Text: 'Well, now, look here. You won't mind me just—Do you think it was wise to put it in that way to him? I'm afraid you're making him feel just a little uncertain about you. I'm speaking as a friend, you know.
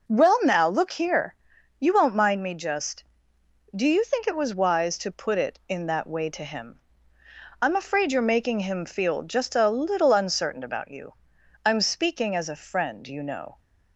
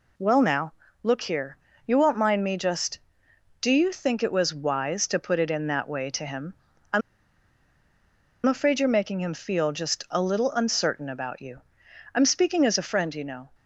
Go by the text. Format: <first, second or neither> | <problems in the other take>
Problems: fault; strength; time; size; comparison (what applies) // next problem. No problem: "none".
first | pauses between "I'm" and "afraid"; strong; at 7.0 s; 1.4 s long